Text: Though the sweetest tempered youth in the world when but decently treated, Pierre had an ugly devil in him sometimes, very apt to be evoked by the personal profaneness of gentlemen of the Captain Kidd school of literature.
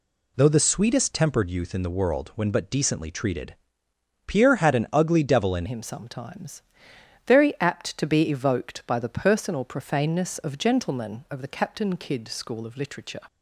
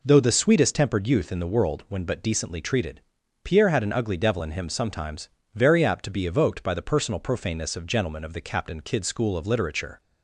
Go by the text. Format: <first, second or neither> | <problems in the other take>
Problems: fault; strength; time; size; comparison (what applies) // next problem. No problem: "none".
second | changes voice at "him"; from 5.6 s on; 7.5 s long